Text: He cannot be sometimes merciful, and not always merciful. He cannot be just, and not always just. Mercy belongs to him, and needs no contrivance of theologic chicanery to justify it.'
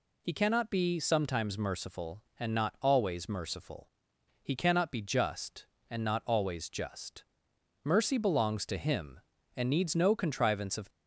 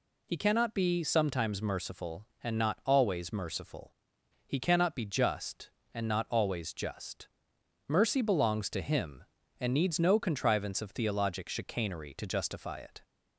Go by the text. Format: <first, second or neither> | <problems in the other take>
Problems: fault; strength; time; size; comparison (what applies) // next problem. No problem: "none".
second | stops before "theologic chicanery to justify it"; at 10.8 s